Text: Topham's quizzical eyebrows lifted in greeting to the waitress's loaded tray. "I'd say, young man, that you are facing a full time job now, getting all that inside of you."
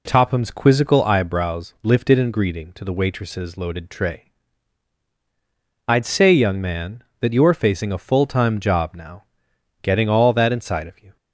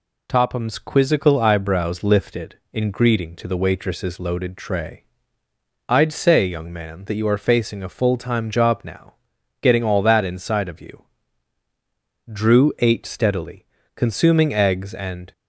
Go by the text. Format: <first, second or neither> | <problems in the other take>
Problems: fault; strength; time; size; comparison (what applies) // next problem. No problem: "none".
first | goes on to say "Drew ate steadily consuming eggs and"; strong; from 12.2 s on; 3.0 s long